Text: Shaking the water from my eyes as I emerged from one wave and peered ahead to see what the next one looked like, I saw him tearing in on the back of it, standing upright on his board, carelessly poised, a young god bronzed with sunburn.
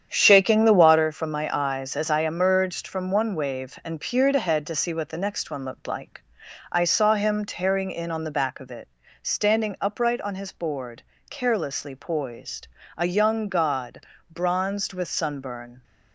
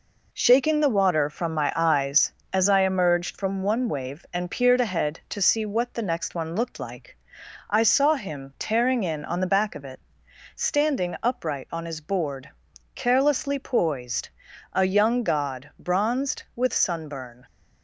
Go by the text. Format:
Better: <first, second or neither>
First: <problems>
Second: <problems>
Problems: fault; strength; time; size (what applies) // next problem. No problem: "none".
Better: second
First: starts louder than the rest; strong; until 1.1 s; 8.5 dB // pauses between "god" and "bronzed"; slight; at 14.0 s; 0.30 s long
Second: none